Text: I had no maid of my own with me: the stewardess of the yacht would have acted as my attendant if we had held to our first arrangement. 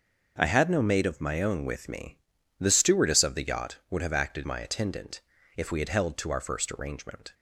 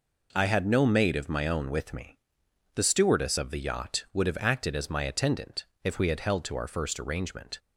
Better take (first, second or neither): second